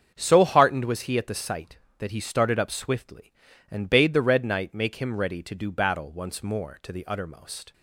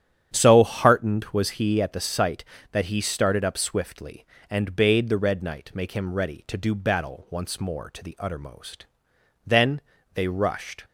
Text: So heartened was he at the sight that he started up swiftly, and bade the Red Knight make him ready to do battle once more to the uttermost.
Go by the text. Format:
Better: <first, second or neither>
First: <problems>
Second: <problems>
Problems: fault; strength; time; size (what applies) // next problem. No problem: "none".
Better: first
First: starts louder than the rest; strong; until 1.1 s; 7.5 dB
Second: starts louder than the rest; strong; until 1.3 s; 9 dB // goes on to say "Then they rushed"; from 9.4 s on; 1.4 s long